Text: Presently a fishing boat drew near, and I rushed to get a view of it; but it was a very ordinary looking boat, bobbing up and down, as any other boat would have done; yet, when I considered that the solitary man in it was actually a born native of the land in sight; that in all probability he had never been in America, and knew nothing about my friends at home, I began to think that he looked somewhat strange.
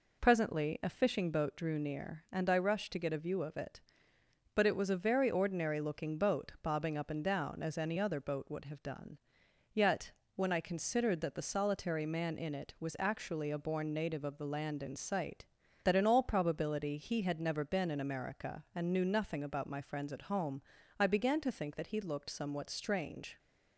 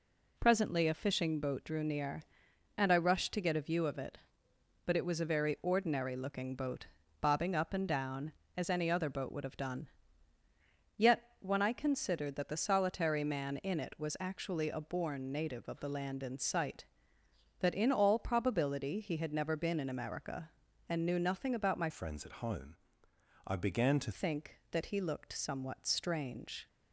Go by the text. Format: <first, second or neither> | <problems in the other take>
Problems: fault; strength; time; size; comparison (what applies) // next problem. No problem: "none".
first | changes voice from "friends" to "to"; from 21.8 to 24.1 s; 2.3 s long